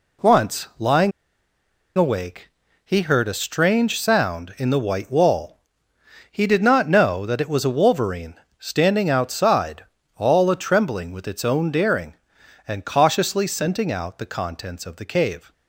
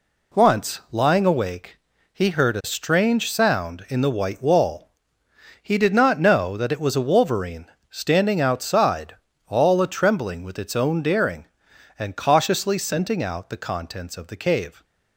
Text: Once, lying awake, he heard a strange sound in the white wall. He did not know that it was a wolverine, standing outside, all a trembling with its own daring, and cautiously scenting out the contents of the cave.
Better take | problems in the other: second | pauses between "lying" and "awake"; noticeable; at 1.1 s; 0.87 s long

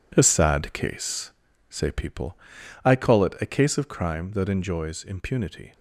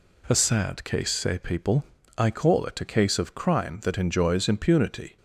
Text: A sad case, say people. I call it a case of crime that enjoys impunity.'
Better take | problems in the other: second | gets quieter; strong; throughout; 9.5 dB

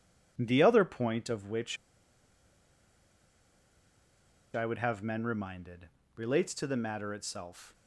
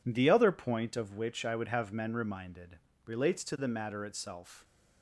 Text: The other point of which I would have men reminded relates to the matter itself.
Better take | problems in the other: second | pauses between "which" and "I"; strong; at 1.7 s; 2.7 s long // pauses between "reminded" and "relates"; slight; at 5.8 s; 0.26 s long; slight in the second

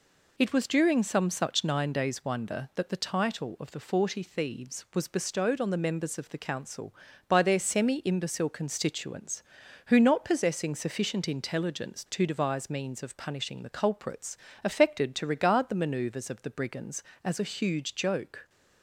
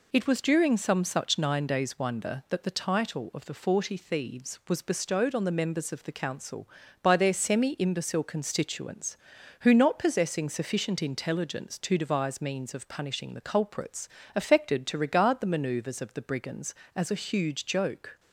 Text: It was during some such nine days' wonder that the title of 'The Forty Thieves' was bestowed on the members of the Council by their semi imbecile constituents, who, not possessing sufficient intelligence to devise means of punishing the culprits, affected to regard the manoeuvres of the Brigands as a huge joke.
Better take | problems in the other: neither | none

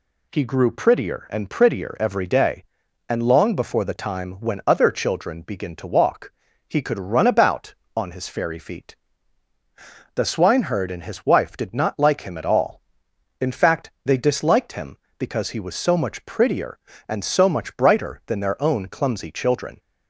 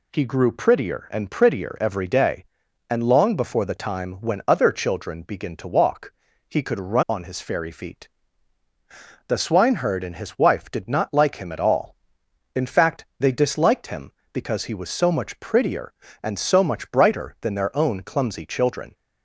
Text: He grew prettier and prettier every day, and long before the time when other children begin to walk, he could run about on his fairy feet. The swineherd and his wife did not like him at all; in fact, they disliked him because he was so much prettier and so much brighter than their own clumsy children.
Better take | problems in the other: first | skips "about"; at 7.0 s

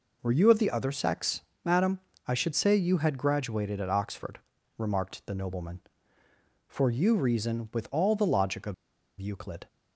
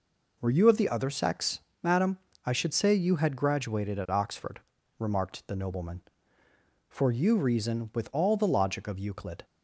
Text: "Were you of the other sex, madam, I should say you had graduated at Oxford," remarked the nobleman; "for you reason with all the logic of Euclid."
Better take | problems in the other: second | pauses between "of" and "Euclid"; noticeable; at 8.7 s; 0.46 s long

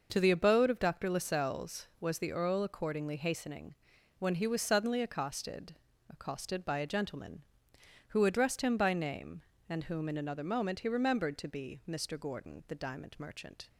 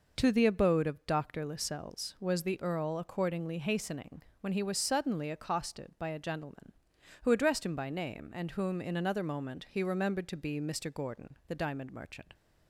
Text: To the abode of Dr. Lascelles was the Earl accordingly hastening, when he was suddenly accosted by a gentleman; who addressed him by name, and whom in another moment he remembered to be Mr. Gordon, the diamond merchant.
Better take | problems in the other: second | says "accosted" twice; at 6.0 s

